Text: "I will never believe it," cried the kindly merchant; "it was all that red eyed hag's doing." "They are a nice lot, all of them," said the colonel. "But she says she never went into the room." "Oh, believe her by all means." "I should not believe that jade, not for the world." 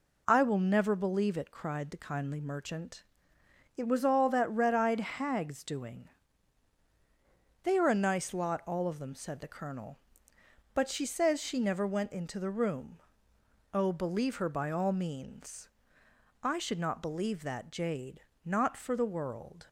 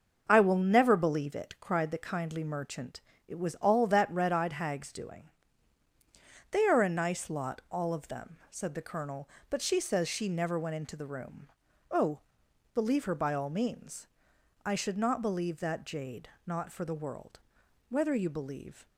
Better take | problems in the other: first | starts louder than the rest; noticeable; until 1.3 s; 6 dB // goes on to say "Whether you believe"; noticeable; from 17.8 s on; 0.98 s long

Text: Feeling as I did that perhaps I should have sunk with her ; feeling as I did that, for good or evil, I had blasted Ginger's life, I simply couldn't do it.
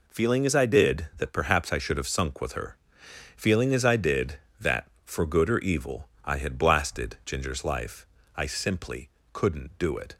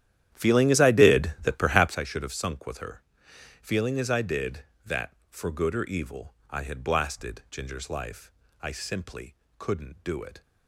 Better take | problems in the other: first | starts louder than the rest; strong; until 2.0 s; 11 dB // pauses between "simply" and "couldn't"; slight; at 9.3 s; 0.24 s long; slight in the first

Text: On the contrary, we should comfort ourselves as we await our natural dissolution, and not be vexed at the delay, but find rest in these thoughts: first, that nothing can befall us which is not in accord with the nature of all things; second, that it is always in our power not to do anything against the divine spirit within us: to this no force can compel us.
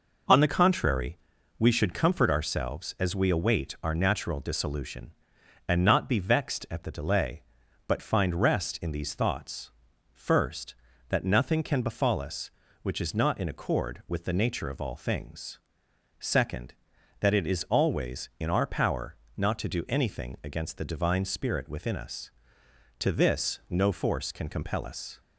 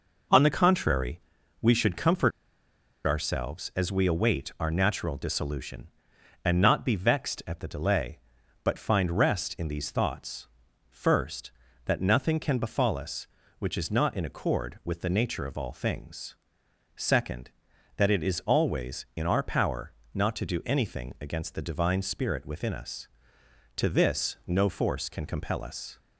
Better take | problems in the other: first | pauses between "comfort" and "ourselves"; noticeable; at 2.3 s; 0.74 s long // pauses between "power" and "not"; slight; at 19.9 s; 0.24 s long; slight in the first

